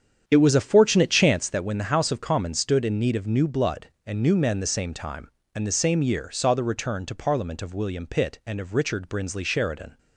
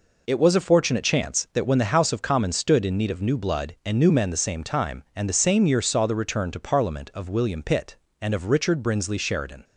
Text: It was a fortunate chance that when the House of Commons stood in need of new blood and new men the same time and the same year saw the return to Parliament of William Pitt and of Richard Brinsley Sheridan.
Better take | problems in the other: second | starts louder than the rest; strong; until 1.4 s; 8.5 dB

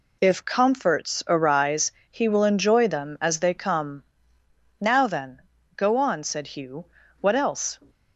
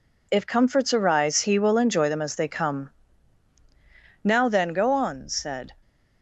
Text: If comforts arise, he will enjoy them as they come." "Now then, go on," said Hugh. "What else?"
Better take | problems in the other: first | stops before "Hugh What else"; at 5.8 s

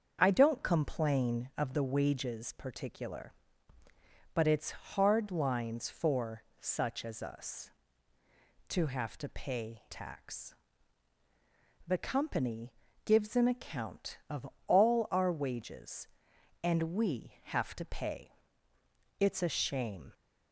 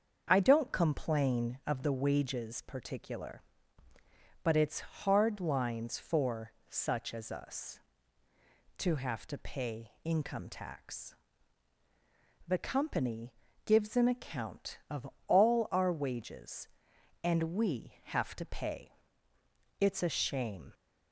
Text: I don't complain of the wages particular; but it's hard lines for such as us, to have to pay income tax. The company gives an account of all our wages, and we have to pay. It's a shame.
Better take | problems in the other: second | starts louder than the rest; until 1.2 s; 6.5 dB; also in the second // pauses between "for" and "such"; slight; at 6.4 s; 0.16 s long; slight in the second // skips "income"; at 9.8 s // pauses between "company" and "gives"; slight; at 12.7 s; 0.32 s long; slight in the second // pauses between "of" and "all"; slight; at 14.4 s; 0.22 s long; slight in the second

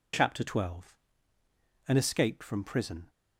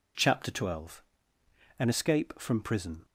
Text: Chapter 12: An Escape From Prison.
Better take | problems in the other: neither | none

